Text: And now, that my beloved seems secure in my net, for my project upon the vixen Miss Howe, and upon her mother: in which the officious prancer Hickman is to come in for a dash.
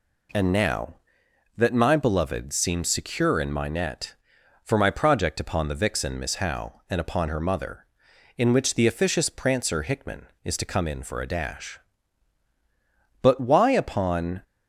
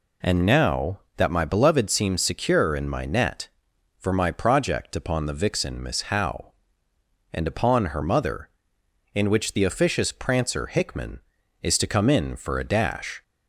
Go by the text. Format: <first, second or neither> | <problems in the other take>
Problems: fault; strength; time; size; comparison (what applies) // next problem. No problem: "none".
second | goes on to say "But why upon"; noticeable; from 13.2 s on; 1.2 s long